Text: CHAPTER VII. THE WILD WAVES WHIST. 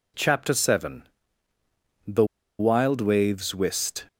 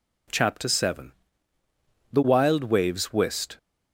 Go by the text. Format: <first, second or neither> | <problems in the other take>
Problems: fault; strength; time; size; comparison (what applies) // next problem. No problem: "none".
second | pauses between "THE" and "WILD"; slight; at 2.2 s; 0.35 s long